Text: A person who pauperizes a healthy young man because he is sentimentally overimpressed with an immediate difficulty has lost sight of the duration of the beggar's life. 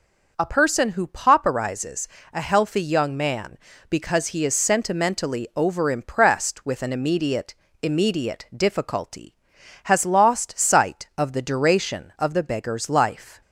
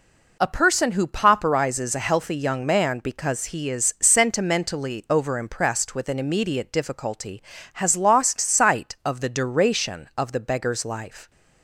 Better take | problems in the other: second | pauses between "pauperizes" and "a"; slight; at 2.0 s; 0.24 s long // says "immediate" twice; at 7.8 s

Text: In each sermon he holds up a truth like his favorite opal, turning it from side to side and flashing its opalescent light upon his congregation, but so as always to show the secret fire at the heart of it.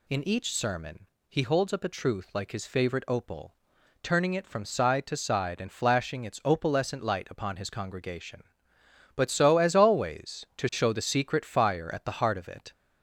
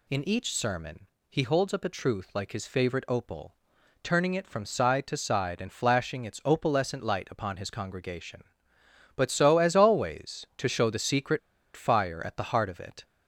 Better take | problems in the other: first | pauses between "sermon" and "he"; slight; at 1.0 s; 0.22 s long; slight in the first // pauses between "secret" and "fire"; slight; at 11.3 s; 0.35 s long

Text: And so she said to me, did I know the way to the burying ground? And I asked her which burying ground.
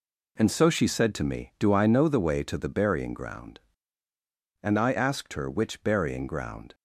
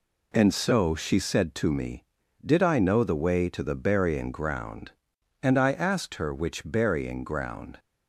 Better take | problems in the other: second | says "do" for "did"; at 1.5 s

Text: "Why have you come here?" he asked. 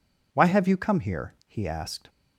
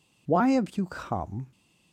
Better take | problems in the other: first | stops before "here he asked"; at 1.5 s

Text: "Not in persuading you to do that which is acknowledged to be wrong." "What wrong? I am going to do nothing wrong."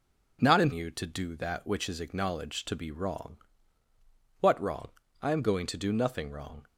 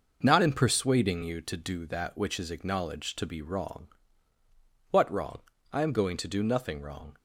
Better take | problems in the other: second | skips "persuading"; at 0.7 s

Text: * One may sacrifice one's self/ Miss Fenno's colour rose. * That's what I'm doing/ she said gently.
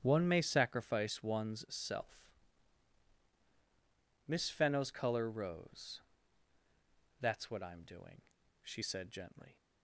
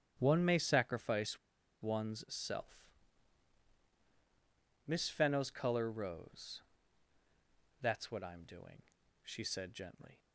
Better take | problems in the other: first | starts louder than the rest; strong; until 1.1 s; 9.5 dB; strong in the first // pauses between "sacrifice" and "one's"; at 1.3 s; 0.43 s long

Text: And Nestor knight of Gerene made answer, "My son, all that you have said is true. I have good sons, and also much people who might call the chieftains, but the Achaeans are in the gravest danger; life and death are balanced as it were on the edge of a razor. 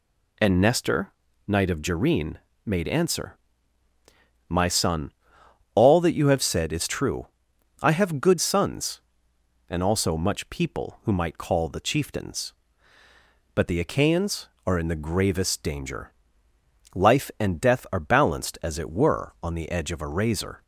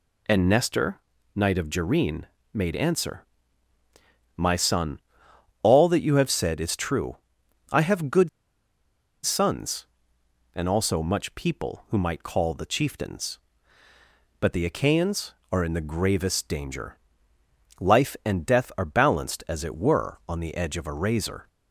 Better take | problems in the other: first | pauses between "Nestor" and "knight"; slight; at 0.9 s; 0.36 s long; slight in the first // pauses between "Gerene" and "made"; slight; at 2.2 s; 0.26 s long; slight in the first // pauses between "good" and "sons"; noticeable; at 8.2 s; 0.96 s long

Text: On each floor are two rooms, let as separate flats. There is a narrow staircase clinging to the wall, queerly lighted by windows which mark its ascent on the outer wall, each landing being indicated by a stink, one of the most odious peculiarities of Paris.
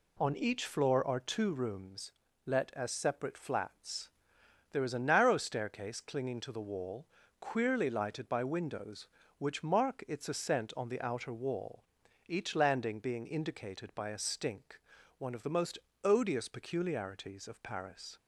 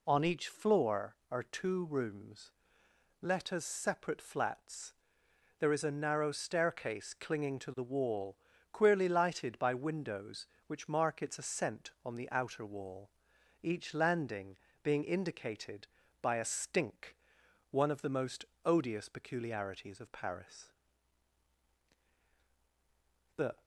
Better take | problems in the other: first | pauses between "landing" and "being"; slight; at 14.5 s; 0.24 s long // pauses between "most" and "odious"; slight; at 18.4 s; 0.22 s long; slight in the first // goes on to say "The"; slight; from 23.3 s on; 0.26 s long

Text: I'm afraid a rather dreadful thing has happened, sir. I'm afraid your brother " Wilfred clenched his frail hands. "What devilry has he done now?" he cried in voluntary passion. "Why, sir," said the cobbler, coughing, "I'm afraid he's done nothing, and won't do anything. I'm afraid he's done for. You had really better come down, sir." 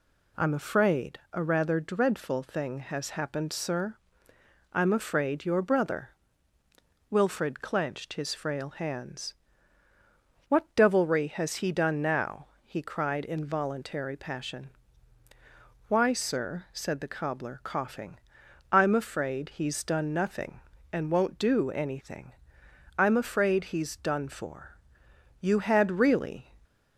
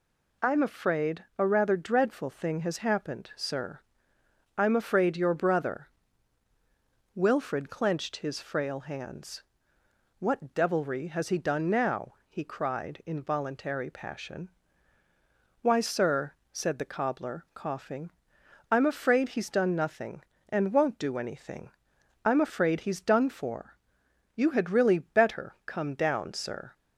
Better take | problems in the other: second | stops before "better come down sir"; at 26.6 s

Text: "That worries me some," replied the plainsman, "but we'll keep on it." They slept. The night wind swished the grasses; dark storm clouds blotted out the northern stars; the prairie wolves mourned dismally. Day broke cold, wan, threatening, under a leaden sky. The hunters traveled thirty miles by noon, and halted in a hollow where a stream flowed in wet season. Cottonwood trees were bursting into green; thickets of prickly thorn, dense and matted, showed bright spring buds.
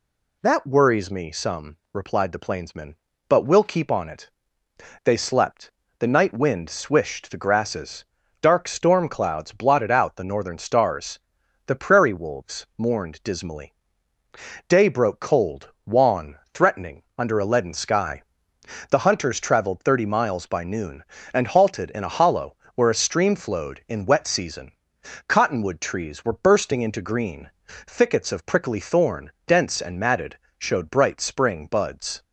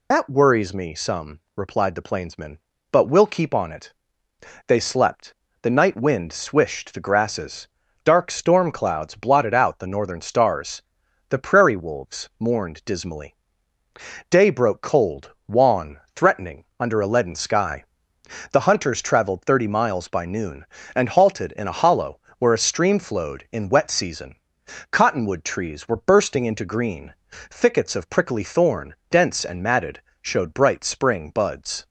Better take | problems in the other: first | loses the start of "That"; at 0.1 s; 65 ms // pauses between "hollow" and "where"; slight; at 22.1 s; 0.20 s long; slight in the first

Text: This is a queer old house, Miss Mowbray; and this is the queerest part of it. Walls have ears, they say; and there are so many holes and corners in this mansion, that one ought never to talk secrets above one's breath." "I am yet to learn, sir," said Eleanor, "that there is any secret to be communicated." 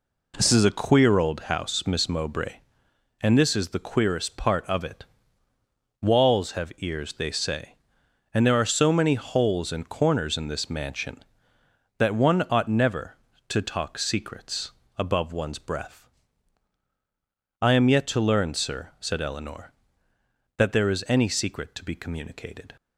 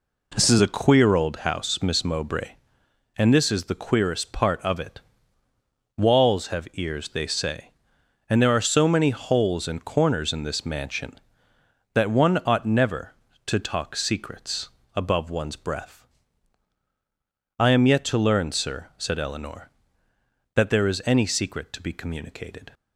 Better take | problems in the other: neither | pauses between "secrets" and "above"; slight; the same in both

